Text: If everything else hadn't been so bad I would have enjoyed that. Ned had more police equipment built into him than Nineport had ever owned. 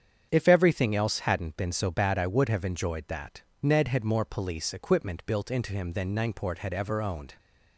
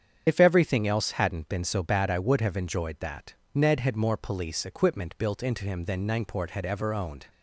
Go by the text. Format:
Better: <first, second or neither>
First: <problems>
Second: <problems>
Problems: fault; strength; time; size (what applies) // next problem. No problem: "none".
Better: first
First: starts louder than the rest; strong; until 1.3 s; 8 dB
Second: loses the start of "If"; at 0.2 s; 50 ms // starts louder than the rest; strong; until 1.2 s; 8 dB